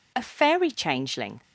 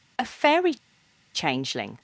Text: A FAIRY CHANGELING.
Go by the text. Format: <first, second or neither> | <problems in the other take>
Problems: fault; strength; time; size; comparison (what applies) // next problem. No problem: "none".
first | pauses between "FAIRY" and "CHANGELING"; noticeable; at 0.7 s; 0.59 s long